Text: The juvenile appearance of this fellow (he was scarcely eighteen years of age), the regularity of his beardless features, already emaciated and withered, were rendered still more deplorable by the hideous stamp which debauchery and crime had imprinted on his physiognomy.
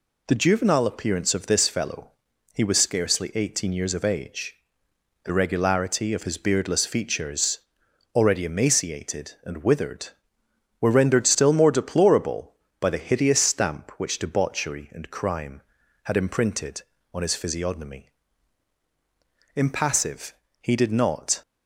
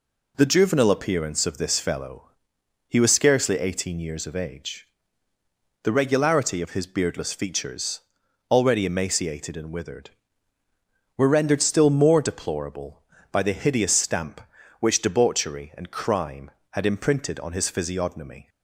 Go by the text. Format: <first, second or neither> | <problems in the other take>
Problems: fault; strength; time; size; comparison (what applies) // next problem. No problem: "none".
second | goes on to say "Impassive he did not"; strong; from 19.5 s on; 1.8 s long